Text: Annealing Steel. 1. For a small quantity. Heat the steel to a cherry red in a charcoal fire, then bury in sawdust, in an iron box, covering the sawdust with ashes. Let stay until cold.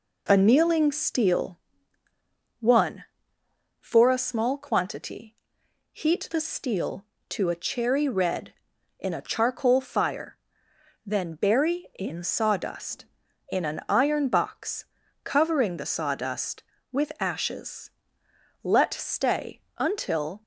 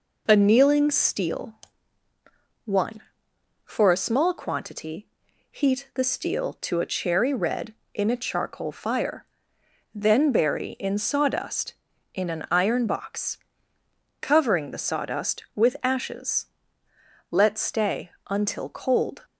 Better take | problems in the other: second | pauses between "stay" and "until"; slight; at 19.6 s; 0.18 s long; slight in the second // stops before "cold"; at 20.4 s

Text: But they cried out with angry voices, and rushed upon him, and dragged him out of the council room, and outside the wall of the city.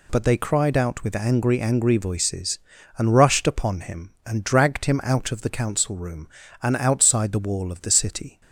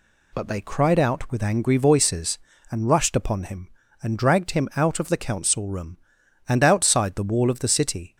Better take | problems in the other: second | says "angry" twice; at 1.6 s

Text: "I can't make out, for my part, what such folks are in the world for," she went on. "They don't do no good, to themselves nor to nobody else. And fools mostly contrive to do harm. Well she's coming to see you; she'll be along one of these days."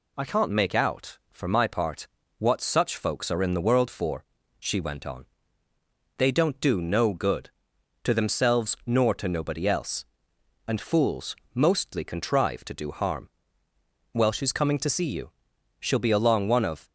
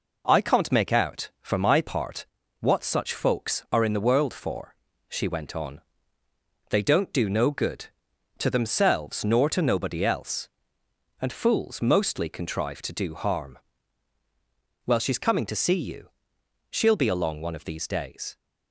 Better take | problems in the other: second | pauses between "fools" and "mostly"; slight; at 11.3 s; 0.20 s long // stops before "these days"; at 16.8 s

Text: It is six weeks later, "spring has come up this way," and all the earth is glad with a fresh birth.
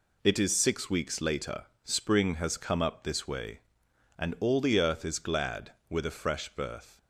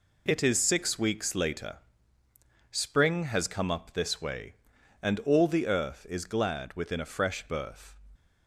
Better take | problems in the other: first | says "within" for "with"; at 6.7 s

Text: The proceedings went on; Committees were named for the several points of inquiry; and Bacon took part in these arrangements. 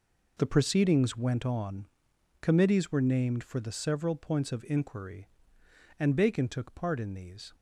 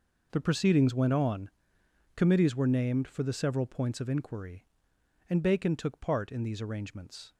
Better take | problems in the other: second | stops before "arrangements"; at 7.5 s

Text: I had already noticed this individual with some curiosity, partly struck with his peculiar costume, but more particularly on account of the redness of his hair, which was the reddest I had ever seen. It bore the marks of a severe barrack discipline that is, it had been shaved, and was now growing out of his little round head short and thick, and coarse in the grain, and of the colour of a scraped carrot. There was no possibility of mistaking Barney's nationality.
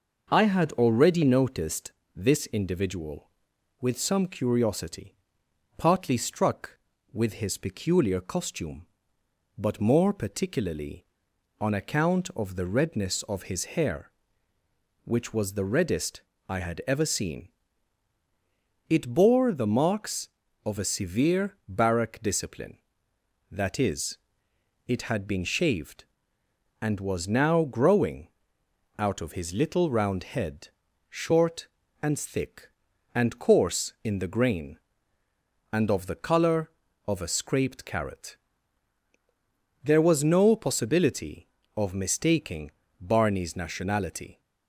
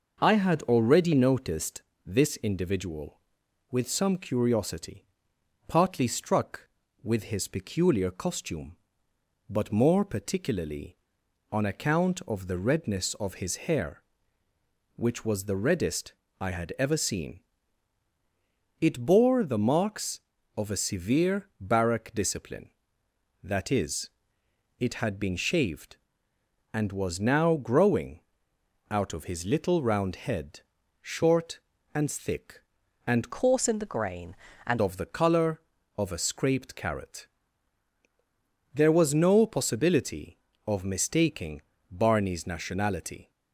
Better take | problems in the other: first | pauses between "noticed" and "this"; slight; at 1.8 s; 0.22 s long; slight in the first // pauses between "reddest" and "I"; slight; at 16.1 s; 0.26 s long; slight in the first // pauses between "growing" and "out"; noticeable; at 28.1 s; 0.70 s long; noticeable in the first // pauses between "head" and "short"; at 30.5 s; 0.40 s long; also in the first // changes voice from "coarse" to "and"; from 33.3 to 34.7 s; 1.4 s long // pauses between "mistaking" and "Barney's"; slight; at 41.6 s; 0.28 s long; slight in the first

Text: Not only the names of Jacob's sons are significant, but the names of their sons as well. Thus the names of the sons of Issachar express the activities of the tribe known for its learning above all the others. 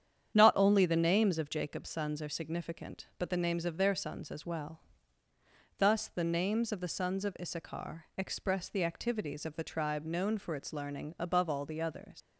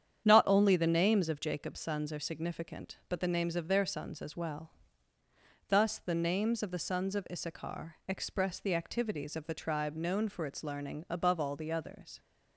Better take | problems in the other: second | starts louder than the rest; strong; until 1.3 s; 9 dB; strong in the second // leaves "others" unfinished; at 12.2 s; 90 ms

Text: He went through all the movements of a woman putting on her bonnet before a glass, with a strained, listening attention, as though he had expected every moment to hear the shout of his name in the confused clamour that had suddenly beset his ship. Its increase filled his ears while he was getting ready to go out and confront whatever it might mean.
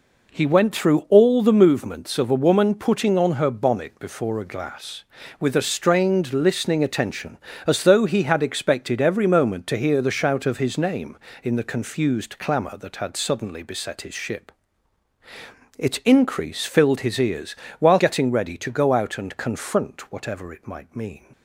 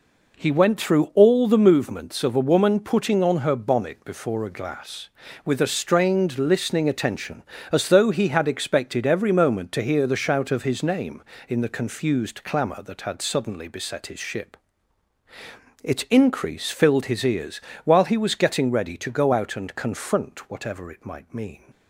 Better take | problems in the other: second | pauses between "ears" and "while"; slight; at 17.5 s; 0.22 s long; slight in the second // skips "he was"; at 17.9 s

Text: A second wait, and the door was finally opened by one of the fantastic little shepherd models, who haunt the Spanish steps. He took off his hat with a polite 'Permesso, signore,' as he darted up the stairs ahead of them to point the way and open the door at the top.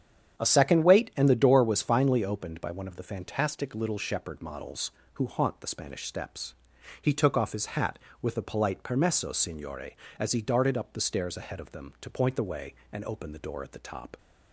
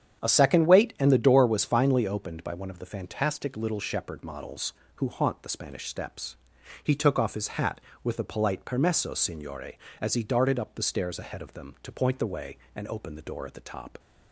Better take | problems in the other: neither | starts louder than the rest; strong; the same in both

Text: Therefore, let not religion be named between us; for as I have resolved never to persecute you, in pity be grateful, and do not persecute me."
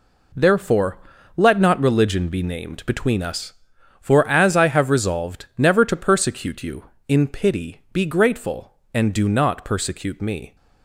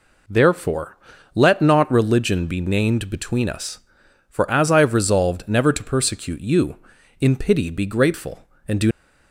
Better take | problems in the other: first | stops before "not persecute me"; at 8.9 s

